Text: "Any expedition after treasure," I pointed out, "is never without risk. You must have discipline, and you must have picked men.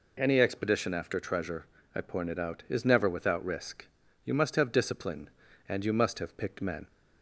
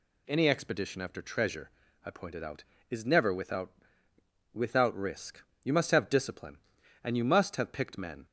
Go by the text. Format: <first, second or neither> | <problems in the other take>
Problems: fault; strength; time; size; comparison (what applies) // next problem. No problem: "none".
first | says "without" twice; at 4.5 s